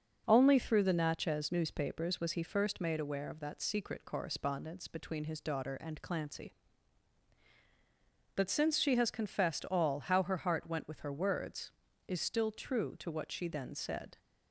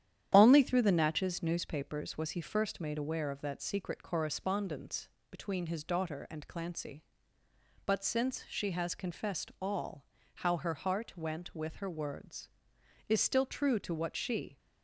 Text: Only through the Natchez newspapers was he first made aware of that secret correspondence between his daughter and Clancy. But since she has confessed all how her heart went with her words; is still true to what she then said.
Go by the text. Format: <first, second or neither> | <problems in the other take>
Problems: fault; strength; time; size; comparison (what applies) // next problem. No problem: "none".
first | starts louder than the rest; strong; until 1.3 s; 10 dB; also in the first // pauses between "correspondence" and "between"; slight; at 5.0 s; 0.22 s long // pauses between "all" and "how"; slight; at 10.0 s; 0.32 s long // stops before "then said"; at 14.5 s